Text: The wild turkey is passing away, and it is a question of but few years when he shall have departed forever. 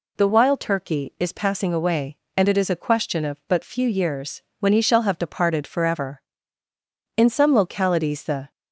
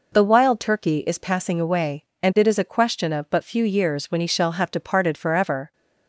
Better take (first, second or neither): second